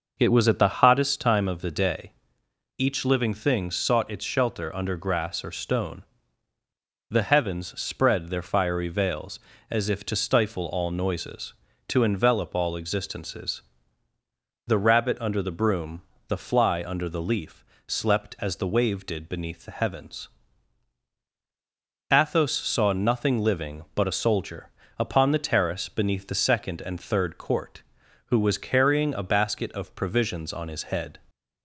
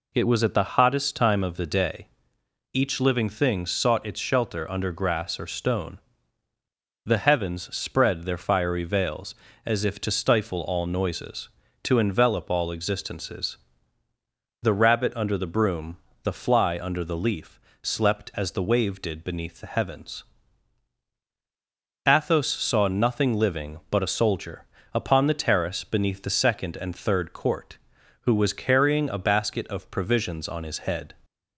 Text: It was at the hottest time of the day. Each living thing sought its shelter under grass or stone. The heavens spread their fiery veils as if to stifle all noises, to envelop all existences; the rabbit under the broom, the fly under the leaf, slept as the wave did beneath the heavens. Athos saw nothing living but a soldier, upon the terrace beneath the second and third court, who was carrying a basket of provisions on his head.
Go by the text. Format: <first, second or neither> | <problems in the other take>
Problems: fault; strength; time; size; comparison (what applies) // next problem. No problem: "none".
second | starts louder than the rest; noticeable; until 1.2 s; 6 dB